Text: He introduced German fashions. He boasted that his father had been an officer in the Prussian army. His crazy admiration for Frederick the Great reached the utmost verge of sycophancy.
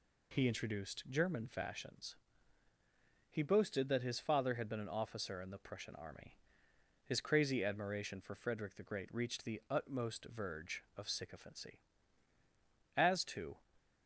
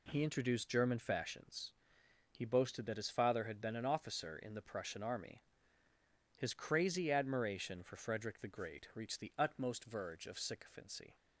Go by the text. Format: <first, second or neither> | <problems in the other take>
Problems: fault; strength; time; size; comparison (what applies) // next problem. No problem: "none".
second | goes on to say "As to"; noticeable; from 12.9 s on; 0.66 s long